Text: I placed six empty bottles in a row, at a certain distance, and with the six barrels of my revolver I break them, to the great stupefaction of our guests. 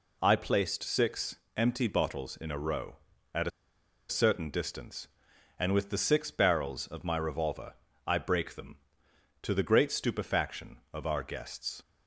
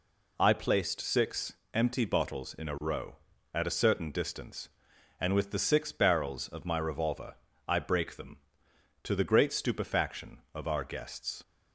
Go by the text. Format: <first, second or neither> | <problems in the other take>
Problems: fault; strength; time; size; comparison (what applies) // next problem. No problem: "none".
second | pauses between "six" and "empty"; slight; at 1.3 s; 0.20 s long; slight in the second // pauses between "a" and "certain"; noticeable; at 3.5 s; 0.60 s long // pauses between "revolver" and "I"; slight; at 7.7 s; 0.32 s long; slight in the second